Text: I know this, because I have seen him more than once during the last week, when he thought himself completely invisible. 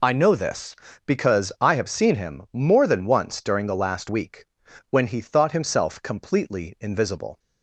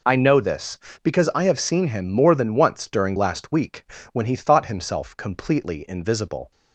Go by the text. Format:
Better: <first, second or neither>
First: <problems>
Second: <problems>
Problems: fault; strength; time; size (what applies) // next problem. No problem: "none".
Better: first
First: none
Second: skips "the"; at 3.1 s